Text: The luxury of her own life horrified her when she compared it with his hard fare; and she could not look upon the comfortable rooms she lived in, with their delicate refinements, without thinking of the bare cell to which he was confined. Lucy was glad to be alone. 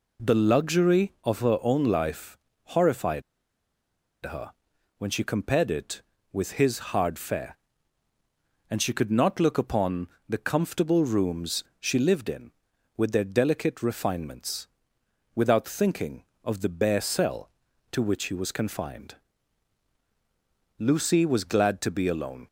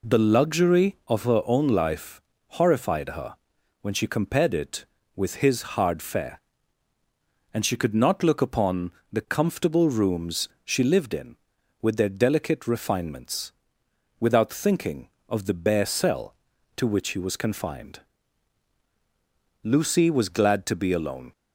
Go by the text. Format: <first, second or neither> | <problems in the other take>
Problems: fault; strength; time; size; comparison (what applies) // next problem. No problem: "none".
second | pauses between "life" and "horrified"; slight; at 2.3 s; 0.28 s long; slight in the second // pauses between "horrified" and "her"; at 3.2 s; 1.0 s long // pauses between "her" and "when"; at 4.5 s; 0.44 s long; also in the second // pauses between "upon" and "the"; slight; at 10.0 s; 0.20 s long; slight in the second // pauses between "rooms" and "she"; slight; at 11.6 s; 0.16 s long; slight in the second